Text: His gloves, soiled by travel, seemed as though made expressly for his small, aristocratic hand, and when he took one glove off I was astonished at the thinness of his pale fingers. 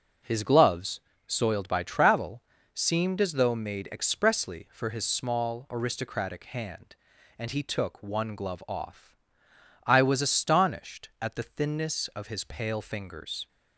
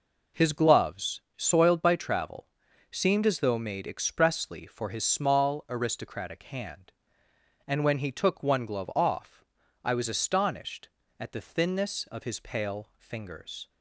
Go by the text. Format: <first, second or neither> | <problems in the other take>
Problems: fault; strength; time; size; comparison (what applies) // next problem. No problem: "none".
second | skips "when"; at 7.5 s // pauses between "off" and "I"; noticeable; at 9.1 s; 0.72 s long; also in the second